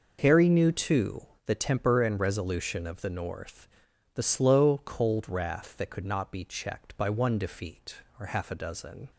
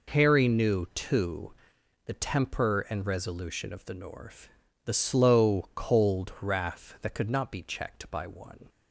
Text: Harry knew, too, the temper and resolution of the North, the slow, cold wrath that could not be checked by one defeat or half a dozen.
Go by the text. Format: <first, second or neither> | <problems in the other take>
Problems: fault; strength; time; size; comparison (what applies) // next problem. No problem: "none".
first | stops before "defeat or half a dozen"; at 8.6 s